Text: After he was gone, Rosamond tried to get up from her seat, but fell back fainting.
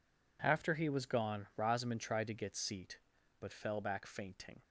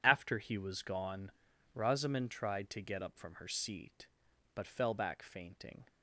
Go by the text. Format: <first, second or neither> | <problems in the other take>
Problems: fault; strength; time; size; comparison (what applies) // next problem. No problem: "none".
second | skips "up from her"; at 2.5 s